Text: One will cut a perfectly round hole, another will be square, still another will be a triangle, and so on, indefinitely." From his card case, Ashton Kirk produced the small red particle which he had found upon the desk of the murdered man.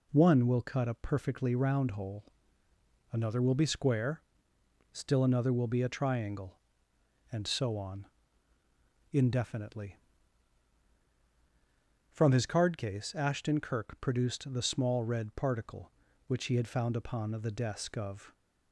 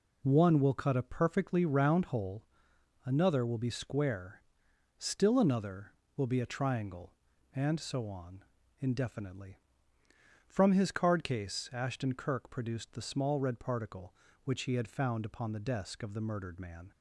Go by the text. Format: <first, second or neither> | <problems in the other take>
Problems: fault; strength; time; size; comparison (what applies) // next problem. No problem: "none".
second | stops before "the murdered man"; at 18.3 s